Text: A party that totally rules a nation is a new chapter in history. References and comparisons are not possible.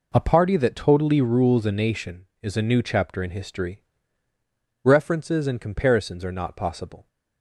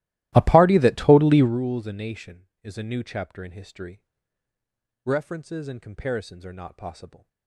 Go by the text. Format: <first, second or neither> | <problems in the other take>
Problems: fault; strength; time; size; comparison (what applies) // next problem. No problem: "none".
first | starts louder than the rest; strong; until 1.6 s; 16 dB